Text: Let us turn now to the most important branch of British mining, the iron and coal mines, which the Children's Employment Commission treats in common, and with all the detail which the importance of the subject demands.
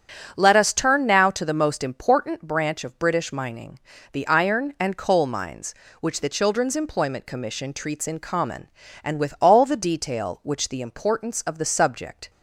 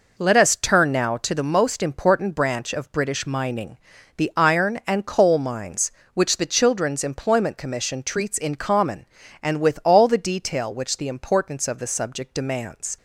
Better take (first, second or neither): second